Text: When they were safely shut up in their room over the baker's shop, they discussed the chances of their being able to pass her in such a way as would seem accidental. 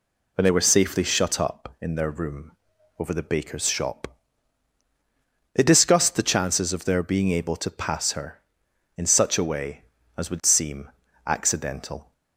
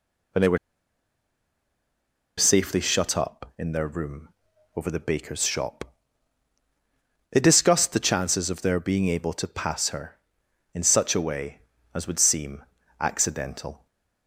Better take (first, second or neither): first